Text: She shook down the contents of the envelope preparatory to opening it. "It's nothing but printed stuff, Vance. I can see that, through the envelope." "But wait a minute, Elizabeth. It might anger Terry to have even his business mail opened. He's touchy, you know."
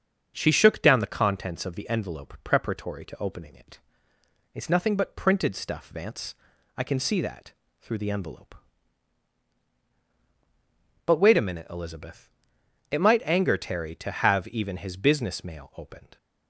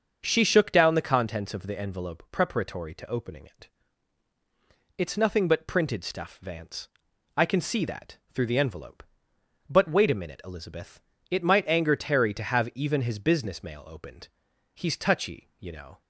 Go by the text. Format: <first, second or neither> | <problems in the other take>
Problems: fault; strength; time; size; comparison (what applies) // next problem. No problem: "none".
second | starts louder than the rest; strong; until 1.3 s; 7 dB; also in the second // stops before "He's touchy you know"; at 16.1 s